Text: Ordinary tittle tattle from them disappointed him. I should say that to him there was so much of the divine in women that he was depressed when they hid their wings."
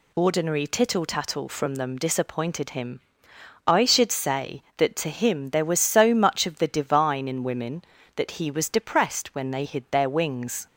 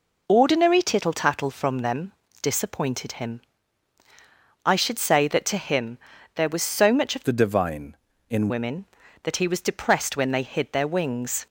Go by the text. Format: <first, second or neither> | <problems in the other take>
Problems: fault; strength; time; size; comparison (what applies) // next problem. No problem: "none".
first | pauses between "them" and "disappointed"; slight; at 2.1 s; 0.30 s long // pauses between "him" and "there"; at 5.9 s; 0.38 s long // changes voice from "the" to "in"; from 7.2 to 8.4 s; 1.2 s long